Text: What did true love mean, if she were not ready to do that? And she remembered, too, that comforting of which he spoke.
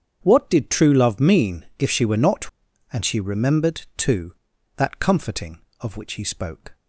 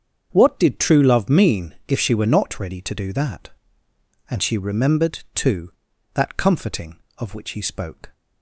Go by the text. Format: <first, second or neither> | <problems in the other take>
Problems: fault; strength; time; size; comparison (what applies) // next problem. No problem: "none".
second | starts louder than the rest; strong; until 1.2 s; 7.5 dB; strong in the second // skips "ready to do that"; at 2.7 s